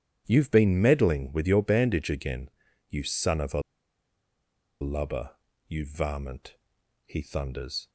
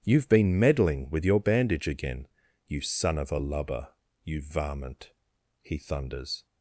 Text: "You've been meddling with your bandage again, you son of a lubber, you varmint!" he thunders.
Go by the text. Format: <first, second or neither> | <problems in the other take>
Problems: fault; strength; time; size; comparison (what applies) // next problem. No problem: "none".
second | starts louder than the rest; strong; until 1.2 s; 10 dB; strong in the second // pauses between "a" and "lubber"; at 3.6 s; 1.2 s long